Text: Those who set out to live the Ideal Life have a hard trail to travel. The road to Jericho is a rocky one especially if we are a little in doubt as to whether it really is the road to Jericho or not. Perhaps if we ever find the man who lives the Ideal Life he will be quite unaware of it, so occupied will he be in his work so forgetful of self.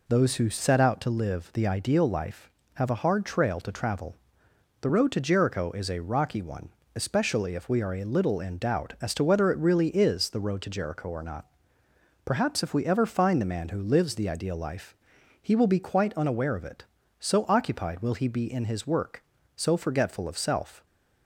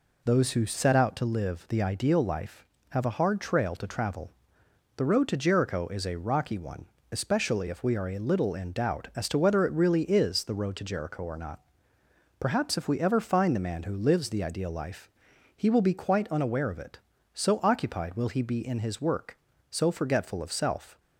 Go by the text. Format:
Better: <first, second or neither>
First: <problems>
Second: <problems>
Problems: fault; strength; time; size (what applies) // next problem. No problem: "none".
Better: neither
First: pauses between "one" and "especially"; slight; at 6.6 s; 0.28 s long // pauses between "Life" and "he"; noticeable; at 14.9 s; 0.46 s long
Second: pauses between "one" and "especially"; slight; at 6.8 s; 0.28 s long // pauses between "Life" and "he"; noticeable; at 15.0 s; 0.46 s long